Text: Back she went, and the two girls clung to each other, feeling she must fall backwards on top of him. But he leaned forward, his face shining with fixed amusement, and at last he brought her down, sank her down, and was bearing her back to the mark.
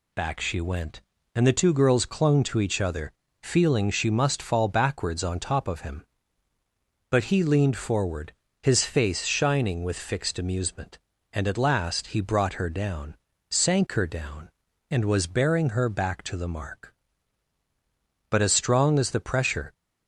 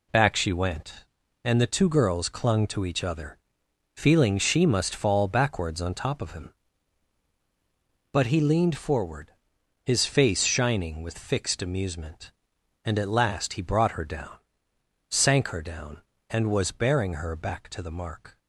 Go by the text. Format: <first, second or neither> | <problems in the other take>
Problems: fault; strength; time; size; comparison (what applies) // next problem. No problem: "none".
second | goes on to say "But as strong as the pressure"; from 18.3 s on; 1.4 s long